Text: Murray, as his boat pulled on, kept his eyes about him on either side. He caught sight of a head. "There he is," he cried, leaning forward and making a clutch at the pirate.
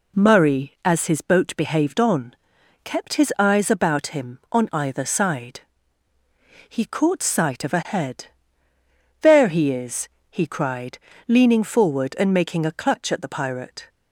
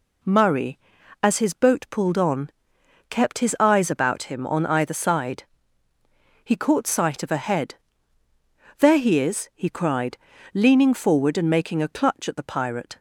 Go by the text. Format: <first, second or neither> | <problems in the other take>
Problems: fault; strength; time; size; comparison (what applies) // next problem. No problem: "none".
second | says "behaved" for "pulled"; at 1.5 s